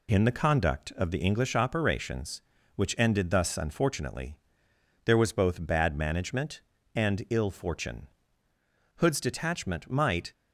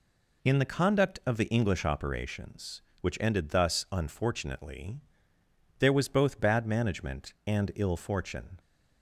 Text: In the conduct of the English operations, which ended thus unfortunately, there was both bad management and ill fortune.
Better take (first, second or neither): second